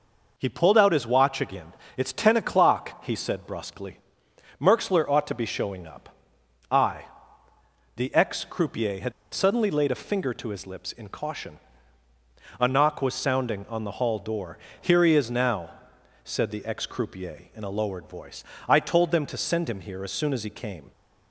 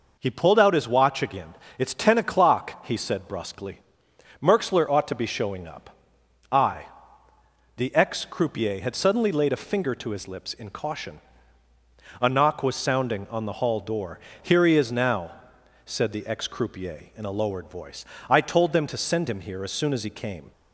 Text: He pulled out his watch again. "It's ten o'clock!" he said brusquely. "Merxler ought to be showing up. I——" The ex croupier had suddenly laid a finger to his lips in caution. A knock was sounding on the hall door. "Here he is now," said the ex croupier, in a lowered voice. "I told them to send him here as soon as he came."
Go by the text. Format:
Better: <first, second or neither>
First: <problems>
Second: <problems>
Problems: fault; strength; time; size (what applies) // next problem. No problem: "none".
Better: second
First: pauses between "had" and "suddenly"; slight; at 9.1 s; 0.21 s long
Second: none